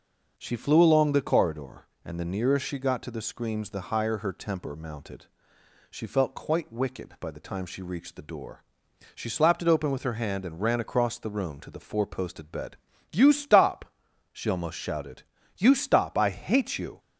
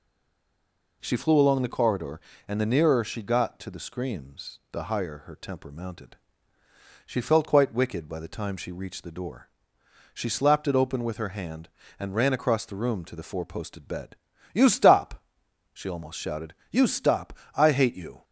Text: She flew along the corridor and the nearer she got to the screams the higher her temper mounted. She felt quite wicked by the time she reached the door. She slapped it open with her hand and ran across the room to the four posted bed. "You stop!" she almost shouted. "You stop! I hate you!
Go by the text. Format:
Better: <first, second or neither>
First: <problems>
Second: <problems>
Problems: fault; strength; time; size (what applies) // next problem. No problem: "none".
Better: first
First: none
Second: stays silent before the first word; until 1.0 s; 1.0 s long